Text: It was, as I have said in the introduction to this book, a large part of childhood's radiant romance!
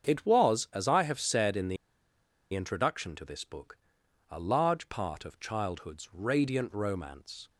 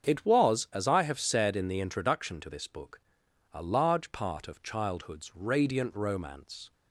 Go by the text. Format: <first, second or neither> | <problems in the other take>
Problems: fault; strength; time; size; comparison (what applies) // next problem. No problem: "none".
second | starts louder than the rest; strong; until 1.1 s; 7 dB; strong in the second // pauses between "the" and "introduction"; noticeable; at 1.7 s; 0.77 s long